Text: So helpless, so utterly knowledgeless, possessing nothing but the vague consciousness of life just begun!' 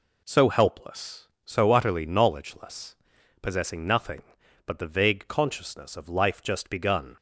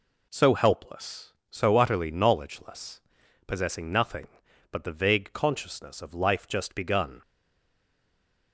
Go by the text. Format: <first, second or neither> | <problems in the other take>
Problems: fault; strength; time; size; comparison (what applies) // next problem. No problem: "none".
first | stays silent after the last word; noticeable; from 7.2 s on; 1.3 s long